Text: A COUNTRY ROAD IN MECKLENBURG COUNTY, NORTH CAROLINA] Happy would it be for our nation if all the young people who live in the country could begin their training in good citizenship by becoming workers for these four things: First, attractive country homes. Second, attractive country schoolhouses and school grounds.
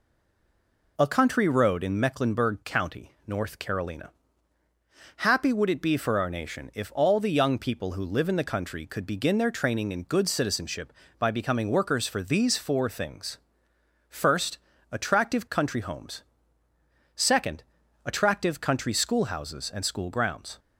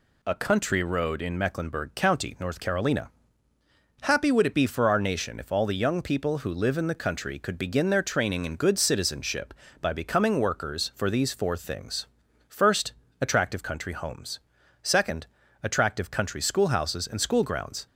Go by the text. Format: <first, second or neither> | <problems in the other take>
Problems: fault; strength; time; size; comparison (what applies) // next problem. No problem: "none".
second | stays silent before the first word; slight; until 0.9 s; 0.9 s long // pauses between "CAROLINA" and "Happy"; at 4.1 s; 1.0 s long; noticeable in the second